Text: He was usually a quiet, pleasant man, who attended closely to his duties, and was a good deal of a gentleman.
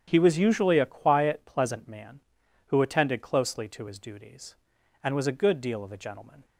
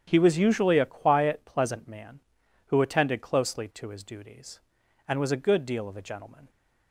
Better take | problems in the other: neither | starts louder than the rest; strong; the same in both

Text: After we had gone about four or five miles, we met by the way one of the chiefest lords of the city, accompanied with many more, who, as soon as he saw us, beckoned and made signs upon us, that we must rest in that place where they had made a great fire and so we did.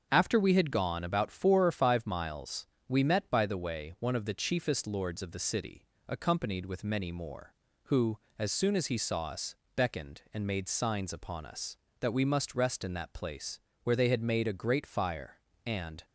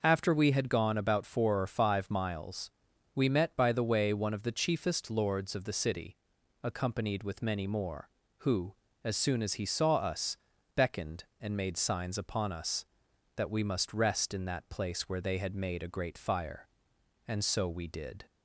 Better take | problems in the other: second | starts louder than the rest; until 1.1 s; 6.5 dB // pauses between "place" and "where"; slight; at 13.5 s; 0.24 s long // stops before "so we did"; at 16.0 s

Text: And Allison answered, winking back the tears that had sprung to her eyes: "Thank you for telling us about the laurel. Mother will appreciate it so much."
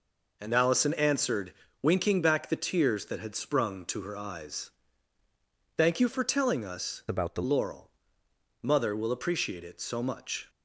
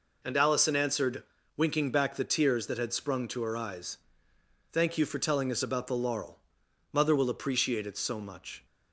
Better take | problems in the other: second | changes voice from "about" to "the"; from 7.0 to 7.4 s; 0.4 s long

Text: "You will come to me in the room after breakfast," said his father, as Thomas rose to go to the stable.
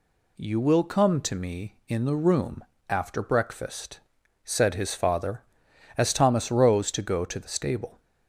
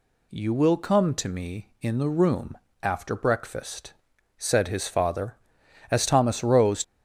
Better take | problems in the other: first | pauses between "room" and "after"; slight; at 2.5 s; 0.26 s long; slight in the first // stops before "to go to the stable"; at 6.8 s

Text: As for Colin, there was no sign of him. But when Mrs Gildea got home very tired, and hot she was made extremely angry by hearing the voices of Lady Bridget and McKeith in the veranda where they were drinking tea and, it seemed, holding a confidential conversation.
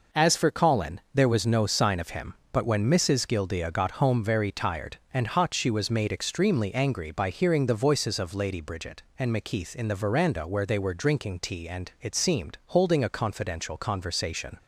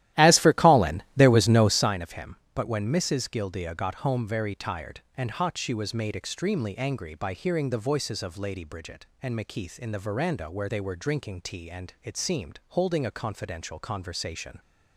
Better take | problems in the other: first | starts louder than the rest; strong; until 1.9 s; 14 dB

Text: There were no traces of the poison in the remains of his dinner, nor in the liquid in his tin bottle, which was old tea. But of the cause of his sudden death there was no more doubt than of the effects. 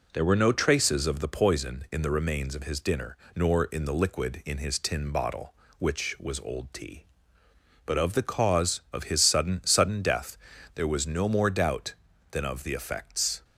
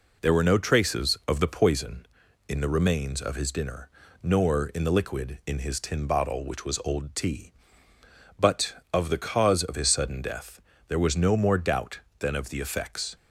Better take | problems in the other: second | says "sudden" twice; at 9.6 s // pauses between "death" and "there"; at 10.3 s; 0.38 s long; slight in the second

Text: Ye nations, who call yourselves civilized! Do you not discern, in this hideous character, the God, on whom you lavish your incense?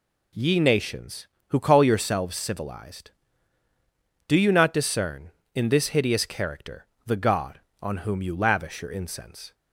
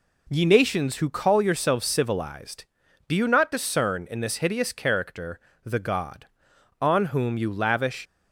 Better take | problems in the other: first | stops before "your incense"; at 8.0 s

